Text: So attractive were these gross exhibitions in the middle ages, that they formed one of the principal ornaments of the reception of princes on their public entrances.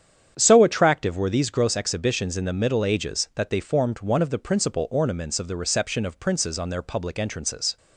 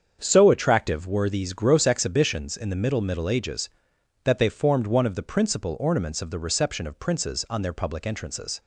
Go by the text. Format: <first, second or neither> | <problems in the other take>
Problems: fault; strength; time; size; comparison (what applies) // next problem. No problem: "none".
first | starts louder than the rest; strong; until 1.2 s; 7 dB; strong in the first // says "middle" twice; at 2.9 s